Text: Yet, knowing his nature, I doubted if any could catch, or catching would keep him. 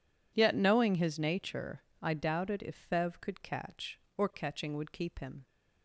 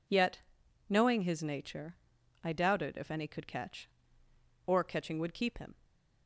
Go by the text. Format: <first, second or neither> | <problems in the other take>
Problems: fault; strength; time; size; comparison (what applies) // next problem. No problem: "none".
second | says "fev" for "any"; at 2.8 s